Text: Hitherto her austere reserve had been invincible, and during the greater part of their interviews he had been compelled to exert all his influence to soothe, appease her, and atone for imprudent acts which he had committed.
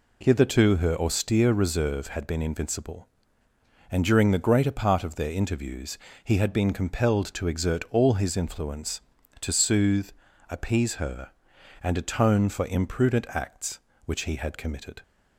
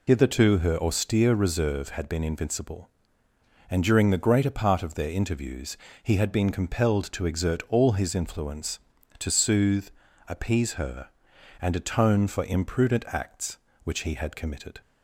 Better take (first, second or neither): first